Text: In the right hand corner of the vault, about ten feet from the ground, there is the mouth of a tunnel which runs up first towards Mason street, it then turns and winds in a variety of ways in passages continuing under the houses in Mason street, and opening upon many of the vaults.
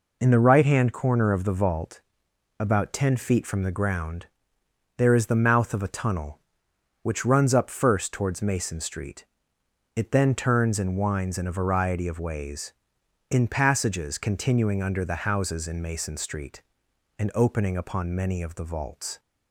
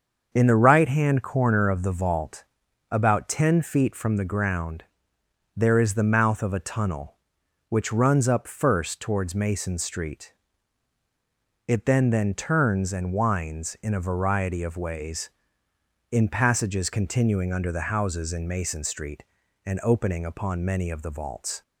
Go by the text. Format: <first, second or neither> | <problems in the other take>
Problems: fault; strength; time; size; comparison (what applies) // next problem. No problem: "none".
first | starts louder than the rest; until 1.3 s; 6.5 dB // says "then" twice; at 12.0 s